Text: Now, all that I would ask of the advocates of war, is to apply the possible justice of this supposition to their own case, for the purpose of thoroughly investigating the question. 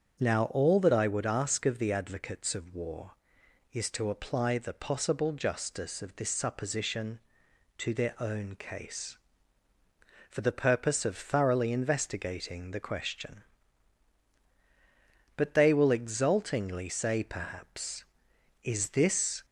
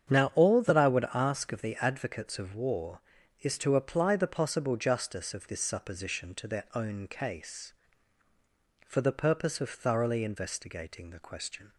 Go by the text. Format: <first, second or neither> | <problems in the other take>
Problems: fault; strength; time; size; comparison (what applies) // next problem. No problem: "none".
second | starts louder than the rest; strong; until 1.2 s; 7 dB; strong in the second // goes on to say "But they will exultingly say perhaps Is this"; strong; from 15.3 s on; 4.0 s long